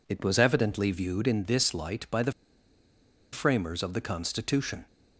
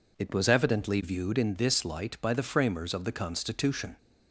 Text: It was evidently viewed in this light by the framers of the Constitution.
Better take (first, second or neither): second